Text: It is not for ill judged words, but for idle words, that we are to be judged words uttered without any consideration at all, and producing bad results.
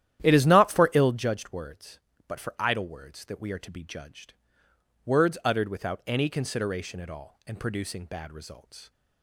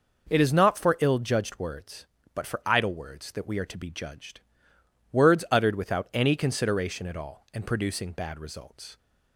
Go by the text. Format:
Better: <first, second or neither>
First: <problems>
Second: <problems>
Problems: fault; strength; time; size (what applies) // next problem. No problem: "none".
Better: second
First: starts louder than the rest; strong; until 1.3 s; 11.5 dB // pauses between "judged" and "words"; noticeable; at 4.3 s; 0.70 s long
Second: pauses between "judged" and "words"; noticeable; at 4.3 s; 0.70 s long